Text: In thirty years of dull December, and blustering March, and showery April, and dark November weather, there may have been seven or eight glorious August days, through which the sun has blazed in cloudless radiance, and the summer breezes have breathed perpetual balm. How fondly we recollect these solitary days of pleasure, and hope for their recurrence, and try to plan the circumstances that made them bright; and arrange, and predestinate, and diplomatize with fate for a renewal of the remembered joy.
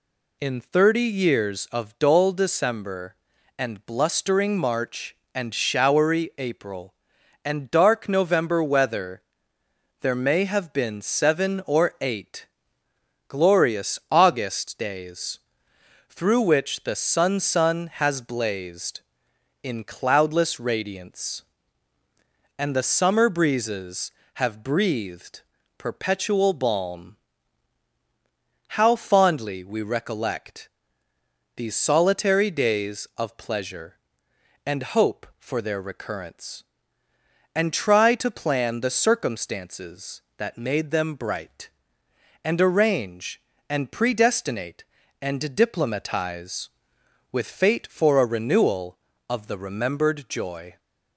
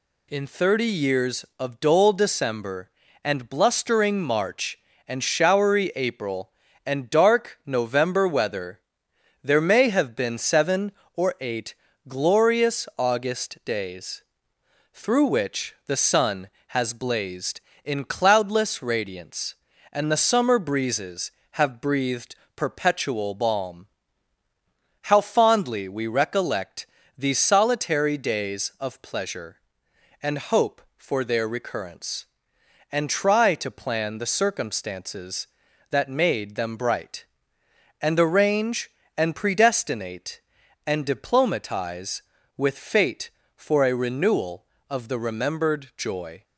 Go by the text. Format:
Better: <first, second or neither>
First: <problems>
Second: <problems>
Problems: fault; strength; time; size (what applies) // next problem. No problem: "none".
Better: second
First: pauses between "eight" and "glorious"; noticeable; at 12.4 s; 0.80 s long // says "sun" twice; at 17.4 s // pauses between "breathed" and "perpetual"; at 25.4 s; 0.38 s long // pauses between "recollect" and "these"; noticeable; at 30.6 s; 0.88 s long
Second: pauses between "eight" and "glorious"; slight; at 11.7 s; 0.34 s long // pauses between "breathed" and "perpetual"; slight; at 22.3 s; 0.20 s long // pauses between "recollect" and "these"; slight; at 26.8 s; 0.32 s long